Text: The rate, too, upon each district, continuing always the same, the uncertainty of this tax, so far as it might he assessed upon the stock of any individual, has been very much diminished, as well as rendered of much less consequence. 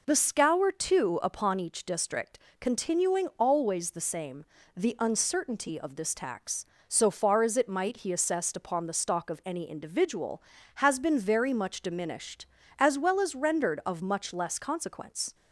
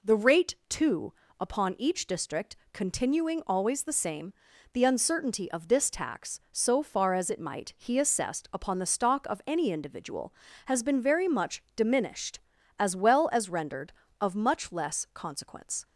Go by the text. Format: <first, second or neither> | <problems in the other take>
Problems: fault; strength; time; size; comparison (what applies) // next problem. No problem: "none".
second | says "scour" for "rate"; at 0.1 s